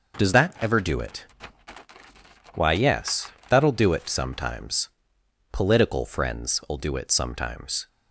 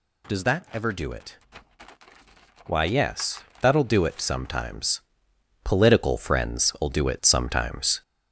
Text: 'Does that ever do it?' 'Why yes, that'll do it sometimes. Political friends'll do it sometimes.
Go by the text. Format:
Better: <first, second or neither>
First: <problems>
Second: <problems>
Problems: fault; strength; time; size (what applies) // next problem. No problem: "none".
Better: first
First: none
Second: gets louder; slight; throughout; 3 dB